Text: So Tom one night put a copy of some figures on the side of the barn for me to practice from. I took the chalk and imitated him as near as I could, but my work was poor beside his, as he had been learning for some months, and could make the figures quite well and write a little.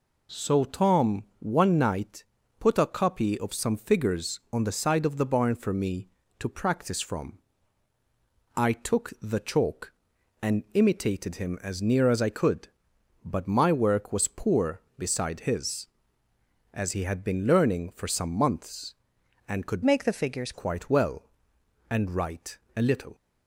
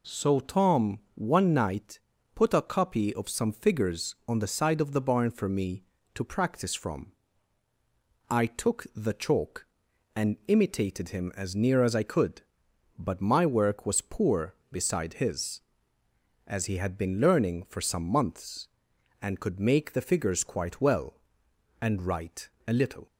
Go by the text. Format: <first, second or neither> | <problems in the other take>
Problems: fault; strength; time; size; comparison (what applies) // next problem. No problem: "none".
second | pauses between "Tom" and "one"; slight; at 1.2 s; 0.16 s long; slight in the second // pauses between "night" and "put"; at 2.2 s; 0.38 s long; also in the second // changes voice from "make" to "figures"; from 19.8 to 20.5 s; 0.7 s long // pauses between "write" and "a"; slight; at 22.5 s; 0.18 s long; slight in the second